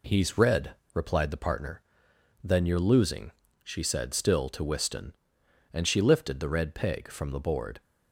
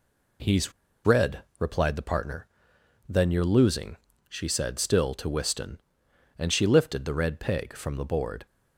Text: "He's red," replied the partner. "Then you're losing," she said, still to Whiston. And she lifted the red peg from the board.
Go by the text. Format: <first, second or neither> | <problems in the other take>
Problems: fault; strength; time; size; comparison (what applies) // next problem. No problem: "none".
first | pauses between "He's" and "red"; slight; at 0.7 s; 0.33 s long